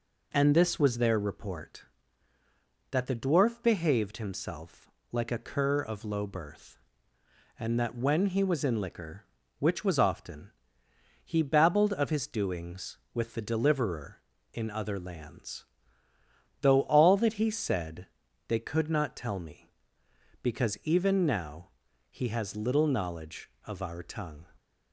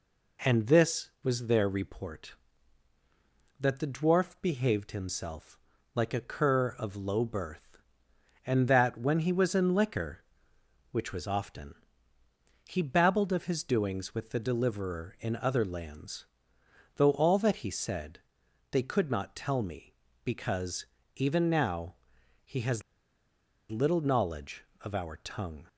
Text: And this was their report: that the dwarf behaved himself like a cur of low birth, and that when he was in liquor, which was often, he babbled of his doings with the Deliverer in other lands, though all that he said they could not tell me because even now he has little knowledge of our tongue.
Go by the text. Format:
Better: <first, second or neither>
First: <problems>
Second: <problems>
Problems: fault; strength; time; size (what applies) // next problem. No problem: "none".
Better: first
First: pauses between "himself" and "like"; slight; at 4.8 s; 0.22 s long // pauses between "said" and "they"; at 18.0 s; 0.44 s long // pauses between "now" and "he"; at 21.6 s; 0.42 s long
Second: pauses between "himself" and "like"; slight; at 5.5 s; 0.36 s long // pauses between "said" and "they"; noticeable; at 18.2 s; 0.50 s long // pauses between "because" and "even"; slight; at 20.8 s; 0.30 s long // pauses between "now" and "he"; noticeable; at 21.9 s; 0.50 s long // pauses between "has" and "little"; noticeable; at 22.8 s; 0.87 s long